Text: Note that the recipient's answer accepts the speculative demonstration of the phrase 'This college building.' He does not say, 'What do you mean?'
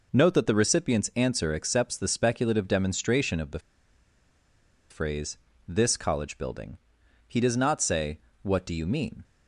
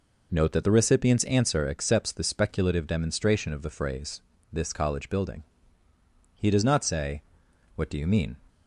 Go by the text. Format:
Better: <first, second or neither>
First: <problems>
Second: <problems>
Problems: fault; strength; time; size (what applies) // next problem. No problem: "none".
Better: second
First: pauses between "the" and "phrase"; strong; at 3.5 s; 1.3 s long // pauses between "phrase" and "This"; slight; at 5.3 s; 0.32 s long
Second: pauses between "phrase" and "This"; slight; at 4.2 s; 0.32 s long